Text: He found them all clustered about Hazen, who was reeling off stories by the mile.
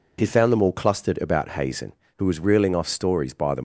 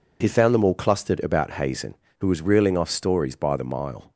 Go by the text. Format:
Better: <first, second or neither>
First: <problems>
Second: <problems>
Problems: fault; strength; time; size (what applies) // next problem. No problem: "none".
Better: second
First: stops before "mile"; at 3.5 s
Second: none